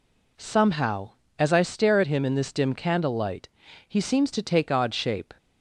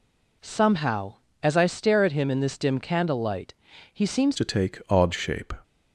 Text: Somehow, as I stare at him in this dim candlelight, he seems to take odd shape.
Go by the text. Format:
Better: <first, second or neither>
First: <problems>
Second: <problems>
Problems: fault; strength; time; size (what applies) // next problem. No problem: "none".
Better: first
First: none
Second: changes voice at "to"; from 4.3 s on; 1.2 s long